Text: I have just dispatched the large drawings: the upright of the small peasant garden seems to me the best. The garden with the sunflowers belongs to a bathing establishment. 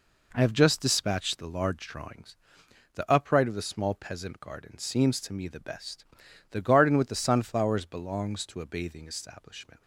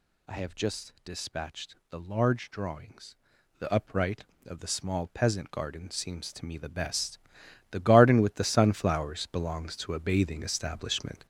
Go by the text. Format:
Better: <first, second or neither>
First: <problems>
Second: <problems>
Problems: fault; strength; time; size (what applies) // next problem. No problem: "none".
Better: first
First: none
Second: gets louder; throughout; 7 dB // pauses between "dispatched" and "the"; slight; at 1.7 s; 0.16 s long